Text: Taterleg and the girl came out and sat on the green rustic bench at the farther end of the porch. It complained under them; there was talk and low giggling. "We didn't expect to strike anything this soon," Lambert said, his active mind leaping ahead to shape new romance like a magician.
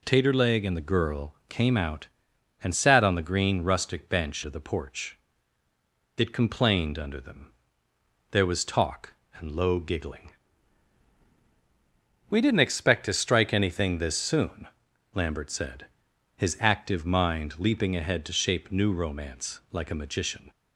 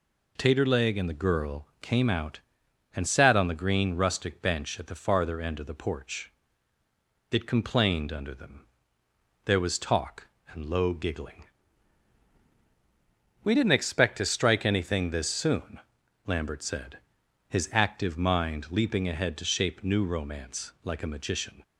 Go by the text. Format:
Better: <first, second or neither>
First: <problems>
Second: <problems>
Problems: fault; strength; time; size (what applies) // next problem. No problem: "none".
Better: second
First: skips "at the farther end"; at 4.4 s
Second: none